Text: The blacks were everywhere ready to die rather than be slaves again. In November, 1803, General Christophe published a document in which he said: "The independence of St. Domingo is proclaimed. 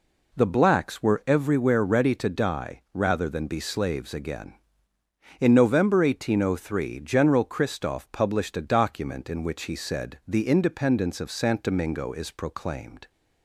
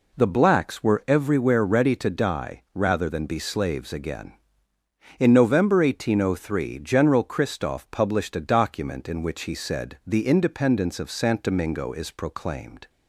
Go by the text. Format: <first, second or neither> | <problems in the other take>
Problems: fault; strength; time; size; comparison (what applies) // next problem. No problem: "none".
neither | none